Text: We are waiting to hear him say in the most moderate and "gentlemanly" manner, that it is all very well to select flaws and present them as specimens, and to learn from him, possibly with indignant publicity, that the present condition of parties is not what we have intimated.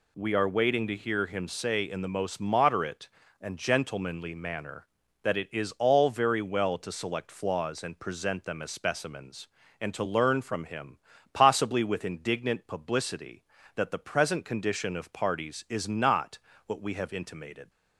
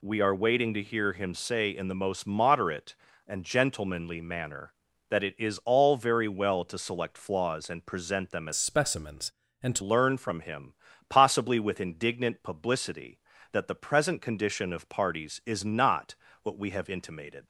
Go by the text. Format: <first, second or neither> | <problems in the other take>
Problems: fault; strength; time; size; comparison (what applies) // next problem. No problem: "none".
first | changes voice from "specimens" to "to"; from 8.5 to 9.8 s; 1.3 s long // pauses between "not" and "what"; slight; at 16.1 s; 0.28 s long; slight in the first